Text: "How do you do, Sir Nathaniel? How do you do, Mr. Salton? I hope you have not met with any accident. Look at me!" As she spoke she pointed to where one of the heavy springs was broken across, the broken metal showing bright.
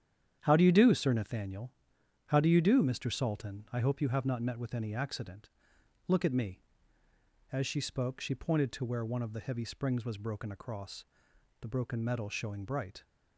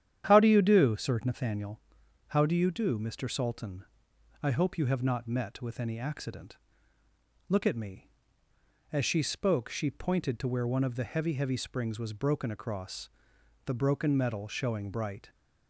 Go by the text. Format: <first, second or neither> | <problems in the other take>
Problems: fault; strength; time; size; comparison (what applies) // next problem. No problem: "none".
first | starts louder than the rest; strong; until 1.3 s; 10 dB; strong in the first // says "heavy" twice; at 11.3 s